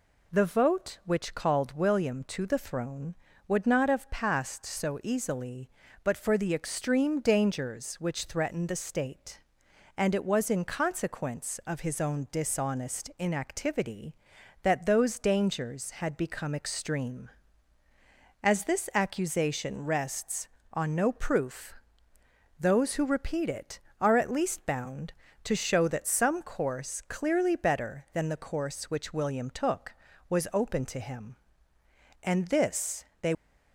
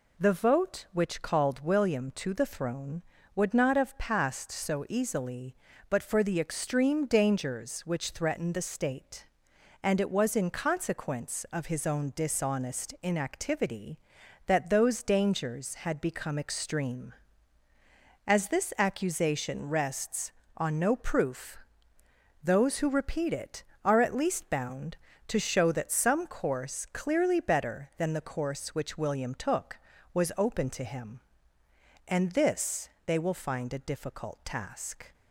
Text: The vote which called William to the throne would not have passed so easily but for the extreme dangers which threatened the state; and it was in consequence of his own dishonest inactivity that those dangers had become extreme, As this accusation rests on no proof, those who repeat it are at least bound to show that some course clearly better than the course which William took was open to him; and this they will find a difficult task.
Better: second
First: pauses between "this" and "they"; slight; at 33.0 s; 0.16 s long // stops before "will find a difficult task"; at 33.3 s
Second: pauses between "this" and "they"; slight; at 32.8 s; 0.16 s long

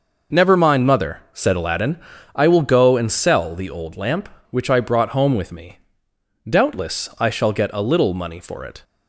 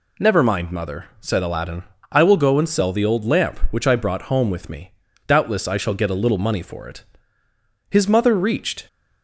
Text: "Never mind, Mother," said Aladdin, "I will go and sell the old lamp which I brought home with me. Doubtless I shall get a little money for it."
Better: first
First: none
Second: goes on to say "His Mother reached"; noticeable; from 7.9 s on; 0.96 s long

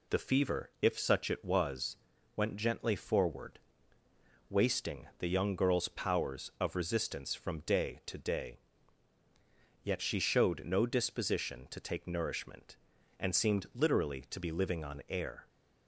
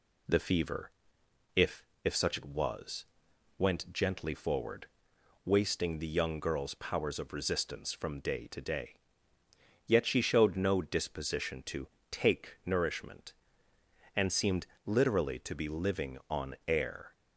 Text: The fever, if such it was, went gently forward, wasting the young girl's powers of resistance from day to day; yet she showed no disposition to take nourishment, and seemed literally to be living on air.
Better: first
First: none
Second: says "if" twice; at 2.0 s // pauses between "to" and "take"; slight; at 11.8 s; 0.24 s long // pauses between "seemed" and "literally"; slight; at 14.6 s; 0.18 s long

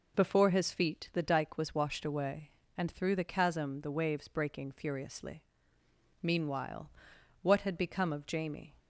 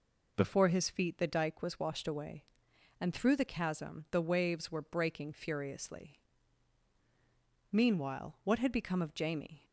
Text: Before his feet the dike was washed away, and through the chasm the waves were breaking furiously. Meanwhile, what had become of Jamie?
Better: second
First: skips "were"; at 4.2 s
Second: none

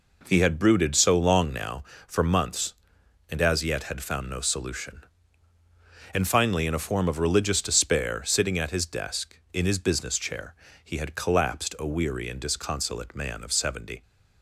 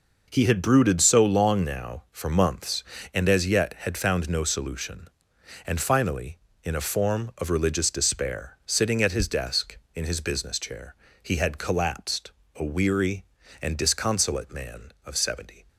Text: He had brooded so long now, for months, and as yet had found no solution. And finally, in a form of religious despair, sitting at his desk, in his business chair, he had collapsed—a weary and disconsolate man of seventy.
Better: neither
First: none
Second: none

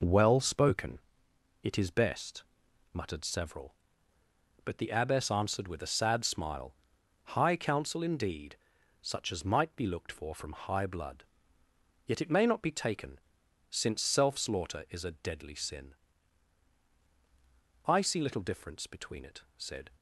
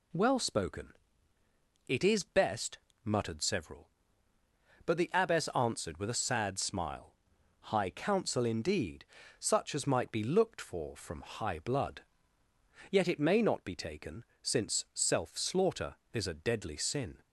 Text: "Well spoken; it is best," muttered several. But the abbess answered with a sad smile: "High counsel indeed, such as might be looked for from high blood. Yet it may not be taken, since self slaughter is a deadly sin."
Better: second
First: goes on to say "I see little difference between it said"; strong; from 17.8 s on; 2.0 s long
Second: none

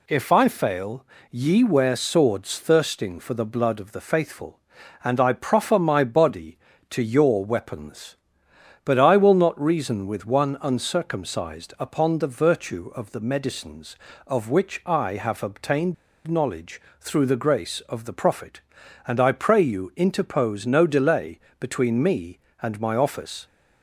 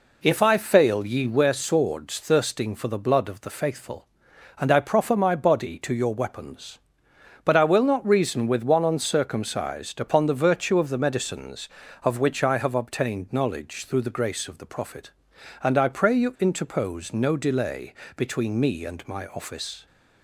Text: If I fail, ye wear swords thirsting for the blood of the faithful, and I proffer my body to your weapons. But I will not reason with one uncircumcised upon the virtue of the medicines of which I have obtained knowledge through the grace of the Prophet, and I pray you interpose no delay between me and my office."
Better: second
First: pauses between "obtained" and "knowledge"; slight; at 15.9 s; 0.32 s long // pauses between "knowledge" and "through"; slight; at 16.8 s; 0.18 s long // pauses between "delay" and "between"; slight; at 21.3 s; 0.22 s long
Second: pauses between "delay" and "between"; slight; at 17.9 s; 0.22 s long

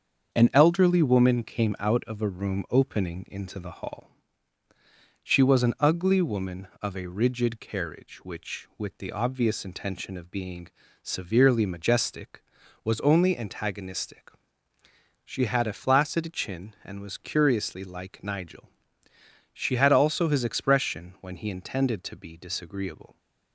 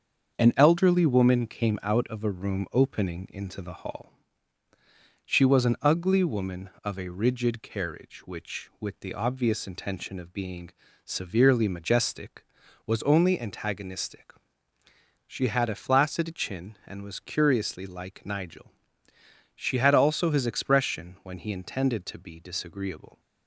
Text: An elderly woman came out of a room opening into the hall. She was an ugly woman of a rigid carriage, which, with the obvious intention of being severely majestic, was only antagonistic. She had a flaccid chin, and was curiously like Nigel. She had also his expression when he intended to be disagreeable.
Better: neither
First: starts louder than the rest; until 1.4 s; 7 dB // pauses between "being" and "severely"; slight; at 10.6 s; 0.34 s long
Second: starts louder than the rest; until 1.4 s; 7 dB // pauses between "being" and "severely"; slight; at 10.7 s; 0.34 s long

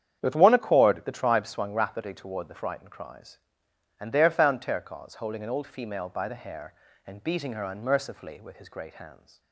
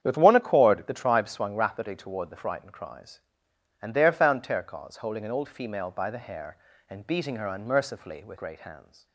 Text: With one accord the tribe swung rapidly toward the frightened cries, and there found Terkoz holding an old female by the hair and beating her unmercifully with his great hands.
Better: first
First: starts louder than the rest; strong; until 1.2 s; 8.5 dB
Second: starts louder than the rest; strong; until 1.0 s; 8.5 dB // skips "his"; at 8.3 s

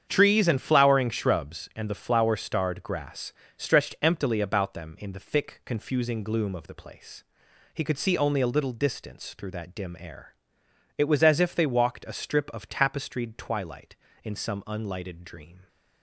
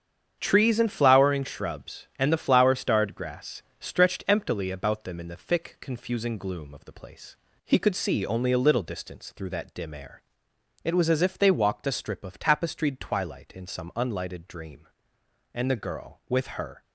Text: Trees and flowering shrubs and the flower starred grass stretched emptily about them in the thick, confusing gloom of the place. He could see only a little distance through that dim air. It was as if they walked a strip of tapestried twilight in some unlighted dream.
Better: first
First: starts louder than the rest; strong; until 1.1 s; 8 dB // pauses between "grass" and "stretched"; slight; at 3.3 s; 0.24 s long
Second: starts louder than the rest; strong; until 1.4 s; 8 dB // pauses between "grass" and "stretched"; slight; at 3.6 s; 0.18 s long // goes on to say "And the girl with her"; noticeable; from 15.5 s on; 1.2 s long

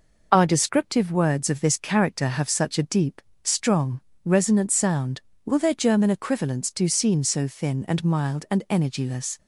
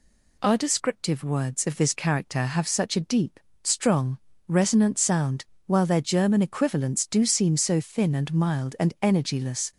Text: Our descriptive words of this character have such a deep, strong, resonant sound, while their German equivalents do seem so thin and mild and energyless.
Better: second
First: says "will" for "while"; at 5.4 s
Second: none

